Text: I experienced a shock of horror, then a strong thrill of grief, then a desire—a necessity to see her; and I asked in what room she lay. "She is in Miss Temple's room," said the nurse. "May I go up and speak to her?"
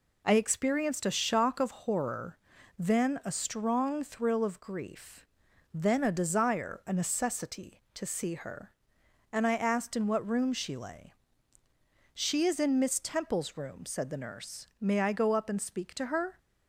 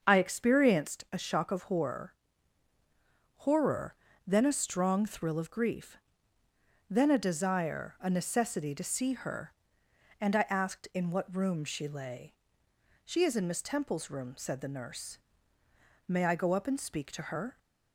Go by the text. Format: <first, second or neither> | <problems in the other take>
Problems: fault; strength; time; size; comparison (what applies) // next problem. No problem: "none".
first | starts louder than the rest; until 1.0 s; 6.5 dB // says "horror" twice; at 3.3 s